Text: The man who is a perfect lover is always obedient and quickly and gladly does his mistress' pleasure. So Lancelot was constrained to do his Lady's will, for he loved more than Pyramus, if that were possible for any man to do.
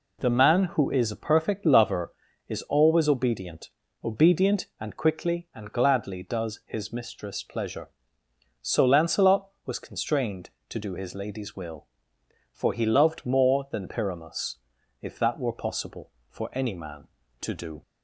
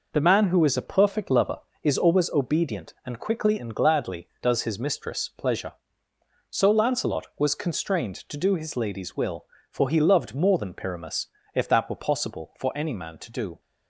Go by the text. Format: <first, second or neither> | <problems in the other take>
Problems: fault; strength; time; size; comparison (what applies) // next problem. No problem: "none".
second | says "obedient" twice; at 4.0 s